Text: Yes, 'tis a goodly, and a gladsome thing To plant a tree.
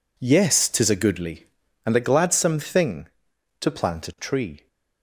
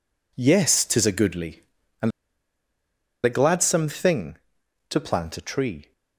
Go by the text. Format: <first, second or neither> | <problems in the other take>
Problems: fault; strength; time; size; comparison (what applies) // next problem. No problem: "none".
first | pauses between "and" and "a"; at 2.1 s; 1.1 s long